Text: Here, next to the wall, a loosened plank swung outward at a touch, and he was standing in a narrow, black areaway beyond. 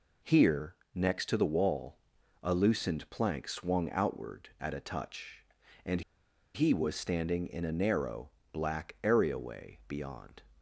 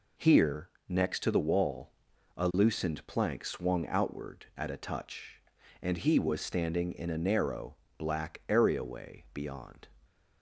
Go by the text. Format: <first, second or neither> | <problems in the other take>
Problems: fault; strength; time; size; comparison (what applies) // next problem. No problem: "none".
second | pauses between "and" and "he"; noticeable; at 6.0 s; 0.54 s long